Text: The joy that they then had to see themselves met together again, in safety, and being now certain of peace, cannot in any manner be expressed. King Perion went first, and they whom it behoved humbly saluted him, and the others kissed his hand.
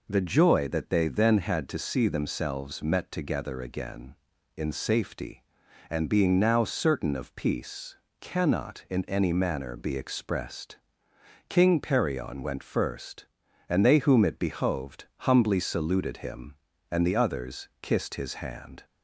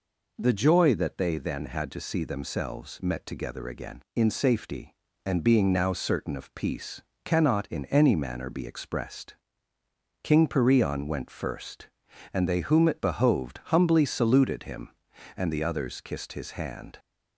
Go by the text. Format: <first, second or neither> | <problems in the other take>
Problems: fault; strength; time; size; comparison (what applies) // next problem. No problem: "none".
neither | none